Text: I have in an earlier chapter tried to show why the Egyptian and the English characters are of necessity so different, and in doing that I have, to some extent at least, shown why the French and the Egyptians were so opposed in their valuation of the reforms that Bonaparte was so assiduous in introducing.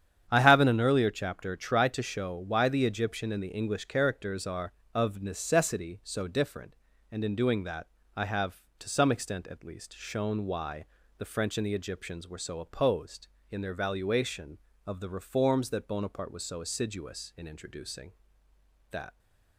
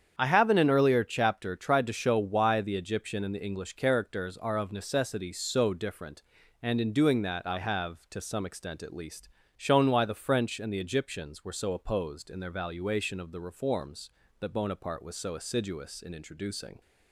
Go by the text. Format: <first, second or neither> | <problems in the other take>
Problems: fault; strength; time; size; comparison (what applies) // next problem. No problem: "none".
second | starts louder than the rest; strong; until 1.3 s; 9 dB; strong in the second // pauses between "that" and "I"; slight; at 7.8 s; 0.28 s long // pauses between "why" and "the"; slight; at 10.8 s; 0.32 s long // goes on to say "That"; slight; from 18.9 s on; 0.28 s long